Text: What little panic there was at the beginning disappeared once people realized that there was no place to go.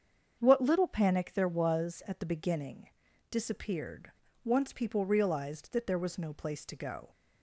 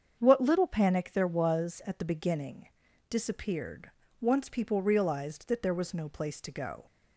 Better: neither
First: starts louder than the rest; strong; until 1.4 s; 7.5 dB // pauses between "beginning" and "disappeared"; at 2.8 s; 0.42 s long // pauses between "disappeared" and "once"; slight; at 4.1 s; 0.30 s long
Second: starts louder than the rest; strong; until 1.2 s; 7.5 dB // pauses between "beginning" and "disappeared"; at 2.6 s; 0.42 s long // pauses between "disappeared" and "once"; slight; at 3.9 s; 0.28 s long

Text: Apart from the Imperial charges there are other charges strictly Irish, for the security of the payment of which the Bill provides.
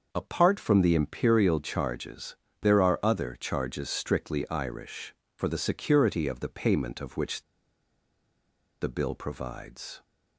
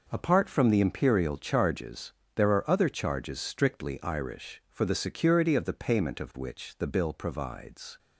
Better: second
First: starts louder than the rest; until 1.1 s; 6 dB // pauses between "charges" and "there"; slight; at 2.3 s; 0.28 s long // pauses between "which" and "the"; strong; at 7.4 s; 1.3 s long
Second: pauses between "charges" and "there"; slight; at 2.1 s; 0.22 s long

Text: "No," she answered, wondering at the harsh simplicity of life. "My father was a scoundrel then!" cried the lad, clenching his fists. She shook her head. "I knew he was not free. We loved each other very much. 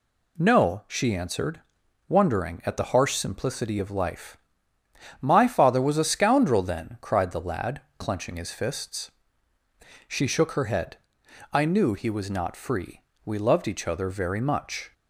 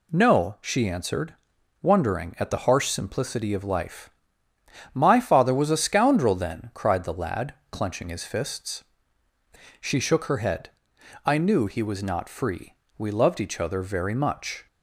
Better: neither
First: none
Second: none

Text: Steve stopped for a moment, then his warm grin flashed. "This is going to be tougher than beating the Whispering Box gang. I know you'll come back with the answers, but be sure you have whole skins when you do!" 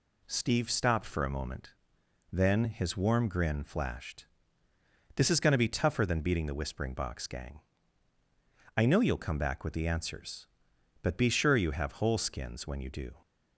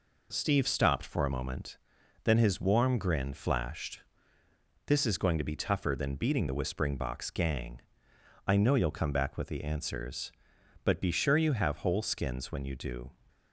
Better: neither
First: none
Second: none

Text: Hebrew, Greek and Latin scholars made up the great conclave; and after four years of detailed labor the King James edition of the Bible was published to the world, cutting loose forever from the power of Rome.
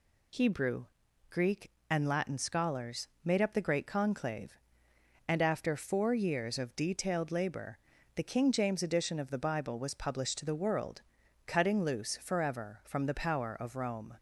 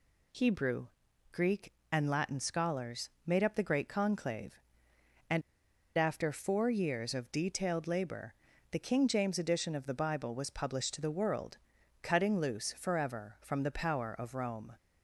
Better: first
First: pauses between "scholars" and "made"; slight; at 3.0 s; 0.18 s long // pauses between "labor" and "the"; slight; at 7.7 s; 0.36 s long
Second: pauses between "scholars" and "made"; slight; at 3.0 s; 0.18 s long // pauses between "and" and "after"; noticeable; at 5.4 s; 0.55 s long // pauses between "labor" and "the"; slight; at 8.3 s; 0.36 s long

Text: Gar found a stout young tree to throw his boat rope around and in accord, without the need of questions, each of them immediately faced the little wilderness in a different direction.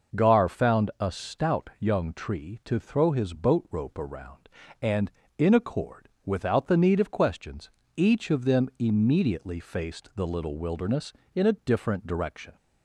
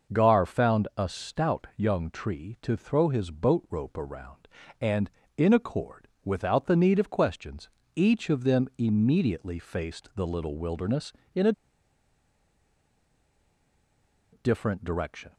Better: first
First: none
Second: pauses between "a" and "different"; strong; at 11.5 s; 2.8 s long

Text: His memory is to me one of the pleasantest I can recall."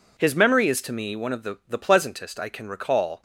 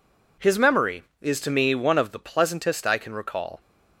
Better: second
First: says "the" twice; at 1.6 s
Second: none

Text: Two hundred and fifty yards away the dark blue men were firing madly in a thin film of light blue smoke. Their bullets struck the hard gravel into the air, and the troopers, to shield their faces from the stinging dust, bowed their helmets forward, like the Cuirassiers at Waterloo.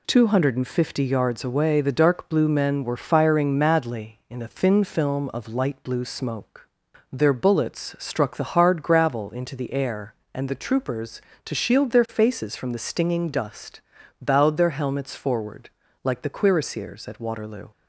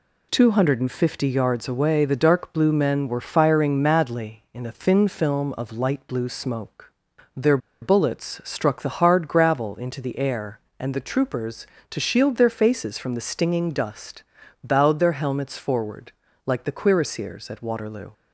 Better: first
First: none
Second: pauses between "Their" and "bullets"; slight; at 7.5 s; 0.24 s long

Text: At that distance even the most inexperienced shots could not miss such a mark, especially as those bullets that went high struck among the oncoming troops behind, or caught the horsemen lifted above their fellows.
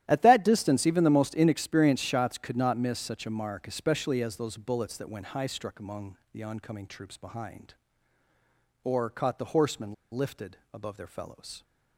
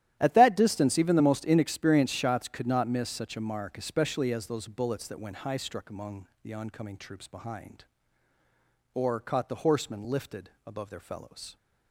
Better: second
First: starts louder than the rest; strong; until 1.0 s; 12.5 dB // pauses between "among" and "the"; slight; at 6.1 s; 0.16 s long // pauses between "horsemen" and "lifted"; slight; at 9.9 s; 0.18 s long // pauses between "lifted" and "above"; slight; at 10.5 s; 0.16 s long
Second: starts louder than the rest; strong; until 1.2 s; 12.5 dB // pauses between "among" and "the"; slight; at 6.2 s; 0.16 s long // pauses between "lifted" and "above"; slight; at 10.4 s; 0.16 s long

